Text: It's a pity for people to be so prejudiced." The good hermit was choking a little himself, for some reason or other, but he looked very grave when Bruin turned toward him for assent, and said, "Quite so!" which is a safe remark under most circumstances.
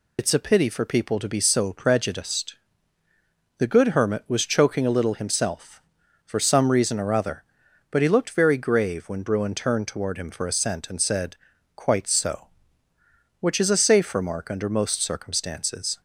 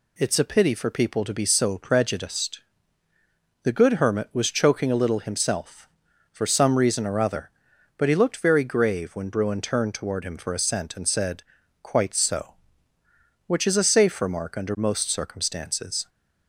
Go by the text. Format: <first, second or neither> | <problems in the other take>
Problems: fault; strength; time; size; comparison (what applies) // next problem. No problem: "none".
second | loses the start of "It's"; at 0.1 s; 60 ms